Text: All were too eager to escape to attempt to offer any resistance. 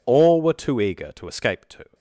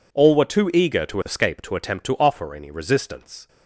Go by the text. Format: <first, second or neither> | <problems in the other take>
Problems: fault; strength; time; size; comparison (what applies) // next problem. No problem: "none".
second | stops before "attempt to offer any resistance"; at 1.9 s